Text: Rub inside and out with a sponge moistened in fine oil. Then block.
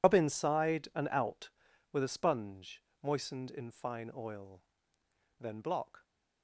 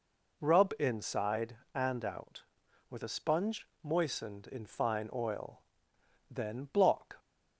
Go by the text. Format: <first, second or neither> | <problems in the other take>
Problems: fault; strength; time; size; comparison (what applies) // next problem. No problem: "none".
second | loses the start of "Rub"; at 0.0 s; 85 ms // pauses between "sponge" and "moistened"; slight; at 2.8 s; 0.22 s long; slight in the second